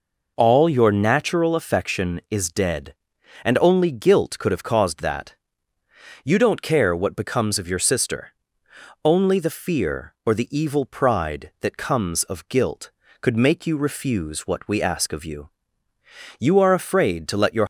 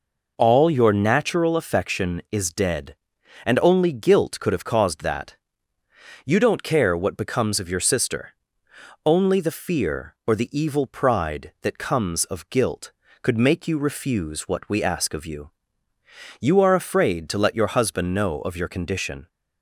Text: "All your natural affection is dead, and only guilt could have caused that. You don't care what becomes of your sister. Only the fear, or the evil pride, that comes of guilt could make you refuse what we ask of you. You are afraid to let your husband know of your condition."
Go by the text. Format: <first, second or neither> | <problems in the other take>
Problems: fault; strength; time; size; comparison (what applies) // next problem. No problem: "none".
second | stops before "husband know of your condition"; at 17.6 s